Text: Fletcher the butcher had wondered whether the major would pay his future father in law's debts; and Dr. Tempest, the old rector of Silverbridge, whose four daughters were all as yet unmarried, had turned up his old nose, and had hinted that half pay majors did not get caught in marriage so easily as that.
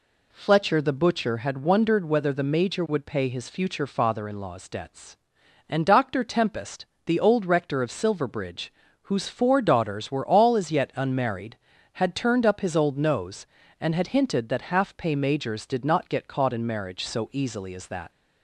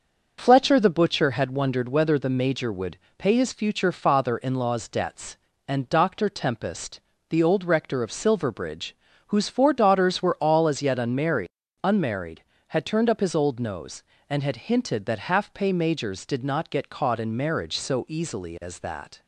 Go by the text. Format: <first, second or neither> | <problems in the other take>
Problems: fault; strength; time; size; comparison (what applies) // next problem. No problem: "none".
first | starts louder than the rest; until 1.4 s; 6.5 dB // pauses between "would" and "pay"; slight; at 2.9 s; 0.20 s long // says "unmarried" twice; at 11.8 s